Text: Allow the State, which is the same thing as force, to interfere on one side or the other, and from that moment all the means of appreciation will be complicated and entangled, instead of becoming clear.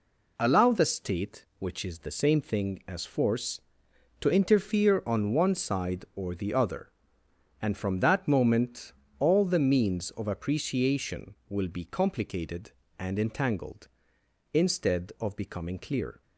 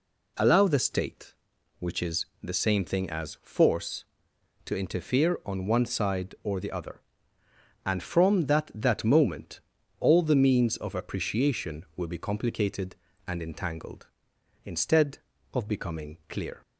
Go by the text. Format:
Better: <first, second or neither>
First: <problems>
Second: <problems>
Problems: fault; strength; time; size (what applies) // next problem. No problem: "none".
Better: first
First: pauses between "moment" and "all"; slight; at 8.9 s; 0.28 s long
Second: pauses between "is" and "the"; slight; at 2.2 s; 0.16 s long // says "that" twice; at 8.7 s // pauses between "moment" and "all"; at 9.5 s; 0.40 s long